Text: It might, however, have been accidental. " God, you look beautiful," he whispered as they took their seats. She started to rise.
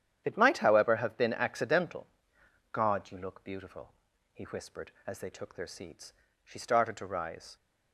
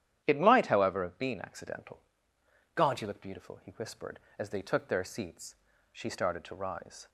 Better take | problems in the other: neither | starts louder than the rest; strong; the same in both

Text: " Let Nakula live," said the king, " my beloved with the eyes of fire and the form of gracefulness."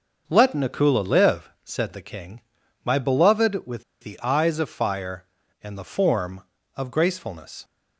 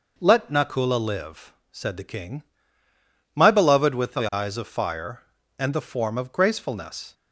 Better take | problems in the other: second | starts louder than the rest; until 1.2 s; 6 dB // pauses between "with" and "the"; slight; at 3.8 s; 0.20 s long

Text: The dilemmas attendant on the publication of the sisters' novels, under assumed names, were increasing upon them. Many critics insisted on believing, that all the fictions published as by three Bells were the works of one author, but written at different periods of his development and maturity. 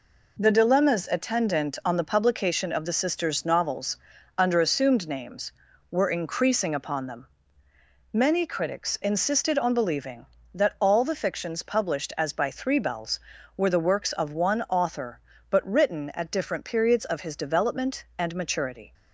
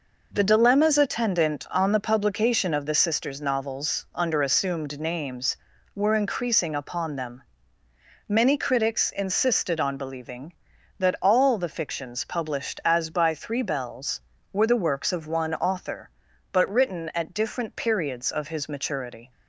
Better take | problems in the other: first | skips "development and"; at 18.6 s

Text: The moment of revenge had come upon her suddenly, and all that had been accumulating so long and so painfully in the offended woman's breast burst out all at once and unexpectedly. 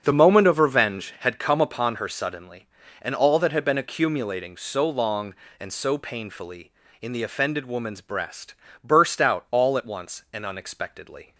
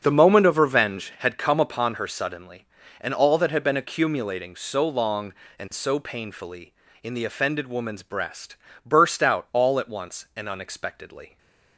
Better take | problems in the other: neither | starts louder than the rest; the same in both // pauses between "breast" and "burst"; slight; the same in both

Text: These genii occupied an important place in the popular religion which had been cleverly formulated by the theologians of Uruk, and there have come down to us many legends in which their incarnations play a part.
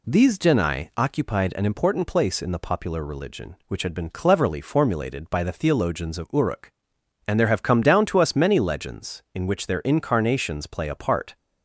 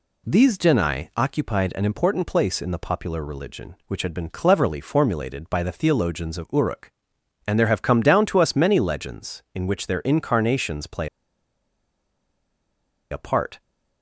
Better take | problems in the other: first | pauses between "play" and "a"; strong; at 11.0 s; 2.0 s long

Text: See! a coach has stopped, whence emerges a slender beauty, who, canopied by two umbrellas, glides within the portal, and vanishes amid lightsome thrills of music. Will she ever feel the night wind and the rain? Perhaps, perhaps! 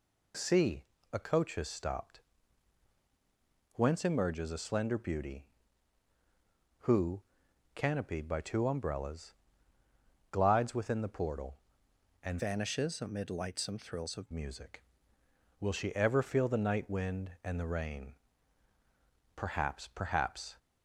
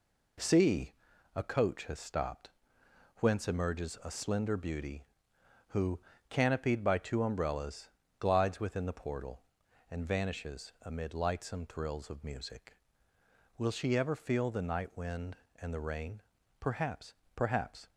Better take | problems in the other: second | changes voice from "vanishes" to "of"; from 12.3 to 14.3 s; 2.0 s long

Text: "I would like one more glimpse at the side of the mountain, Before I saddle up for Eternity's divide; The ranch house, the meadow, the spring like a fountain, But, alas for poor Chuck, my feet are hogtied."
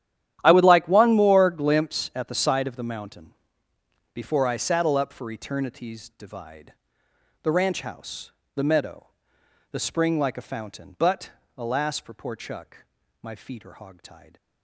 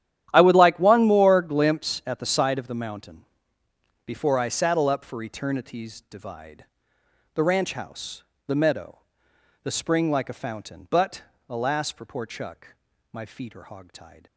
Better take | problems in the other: neither | starts louder than the rest; strong; the same in both

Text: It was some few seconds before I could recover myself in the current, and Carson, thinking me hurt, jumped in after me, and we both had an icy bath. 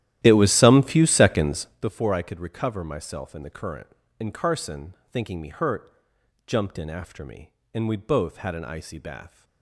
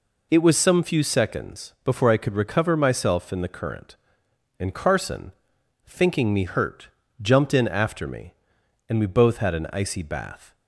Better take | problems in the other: second | starts louder than the rest; strong; until 1.9 s; 13 dB

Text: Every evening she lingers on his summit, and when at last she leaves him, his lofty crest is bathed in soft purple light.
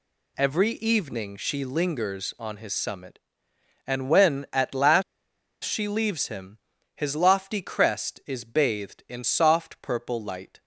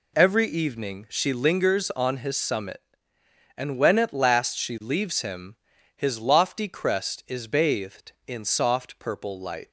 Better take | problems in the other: second | pauses between "last" and "she"; noticeable; at 5.0 s; 0.61 s long

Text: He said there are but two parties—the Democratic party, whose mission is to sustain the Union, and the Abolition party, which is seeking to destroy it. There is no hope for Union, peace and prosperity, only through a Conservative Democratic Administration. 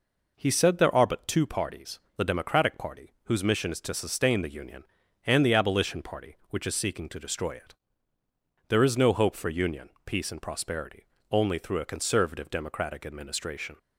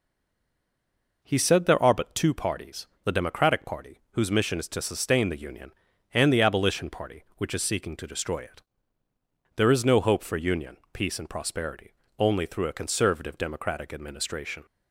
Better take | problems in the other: first | stays silent before the first word; noticeable; until 1.2 s; 1.2 s long

